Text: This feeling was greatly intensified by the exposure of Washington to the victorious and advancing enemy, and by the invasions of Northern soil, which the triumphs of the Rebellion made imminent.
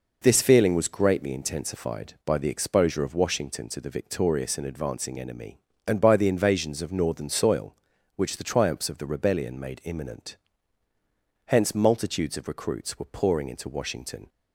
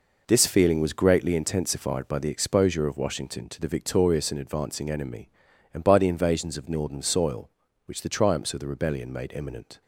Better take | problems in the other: second | goes on to say "Hence multitudes of recruits were pouring into Washington"; strong; from 11.4 s on; 2.8 s long

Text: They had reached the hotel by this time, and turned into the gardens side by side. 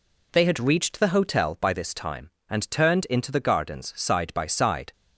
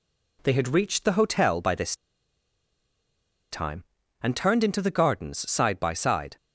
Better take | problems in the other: first | pauses between "this" and "time"; strong; at 1.9 s; 1.5 s long

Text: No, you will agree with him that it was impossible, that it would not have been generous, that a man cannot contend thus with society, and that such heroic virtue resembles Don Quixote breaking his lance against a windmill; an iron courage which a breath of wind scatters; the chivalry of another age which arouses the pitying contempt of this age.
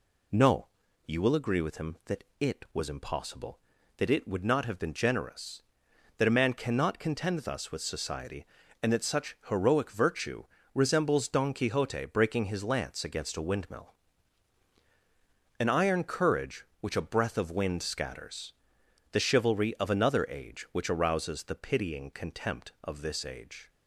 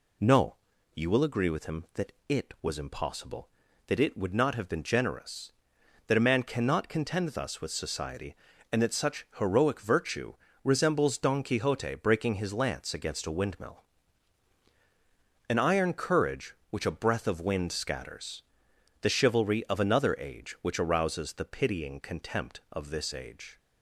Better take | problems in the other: neither | pauses between "that" and "it"; slight; the same in both // pauses between "virtue" and "resembles"; slight; the same in both

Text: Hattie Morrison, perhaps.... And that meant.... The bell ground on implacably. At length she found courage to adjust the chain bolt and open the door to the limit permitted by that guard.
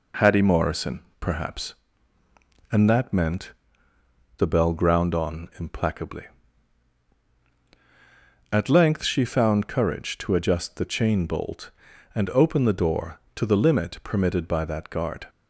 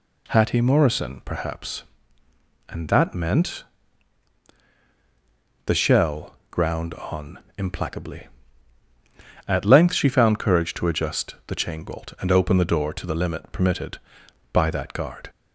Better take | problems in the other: first | says "shell" for "bell"; at 5.7 s // pauses between "on" and "implacably"; slight; at 7.3 s; 0.18 s long

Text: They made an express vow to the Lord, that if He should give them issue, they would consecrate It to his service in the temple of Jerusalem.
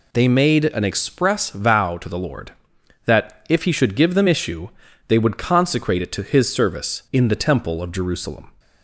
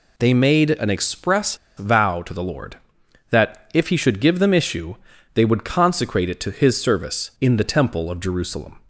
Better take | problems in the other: first | pauses between "express" and "vow"; slight; at 1.5 s; 0.20 s long

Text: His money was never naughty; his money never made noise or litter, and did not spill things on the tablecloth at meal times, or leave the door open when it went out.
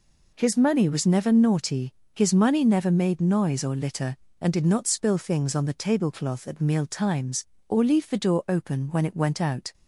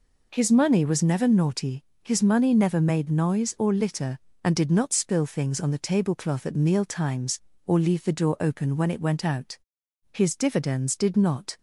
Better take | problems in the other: first | goes on to say "His dividends did not"; from 10.1 s on; 1.4 s long

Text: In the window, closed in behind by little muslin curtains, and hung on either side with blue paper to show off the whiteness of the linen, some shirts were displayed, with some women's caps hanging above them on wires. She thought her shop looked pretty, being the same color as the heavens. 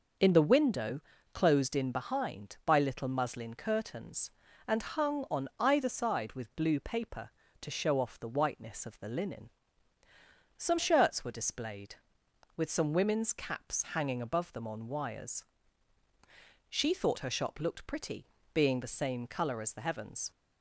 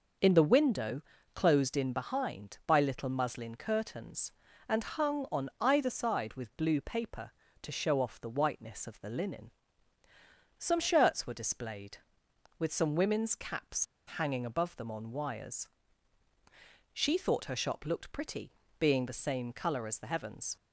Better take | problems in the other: first | pauses between "caps" and "hanging"; slight; at 13.8 s; 0.31 s long

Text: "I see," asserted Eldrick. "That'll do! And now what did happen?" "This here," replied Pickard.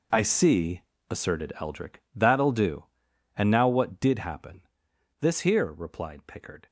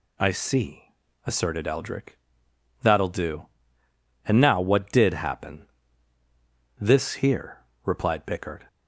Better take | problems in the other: second | gets quieter; strong; throughout; 14 dB

